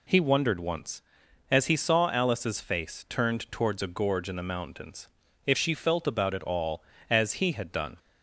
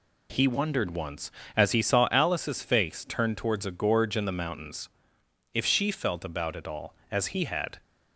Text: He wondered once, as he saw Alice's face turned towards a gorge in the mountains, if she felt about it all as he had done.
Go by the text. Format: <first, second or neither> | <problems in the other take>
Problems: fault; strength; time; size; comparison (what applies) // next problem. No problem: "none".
first | stops before "done"; at 7.8 s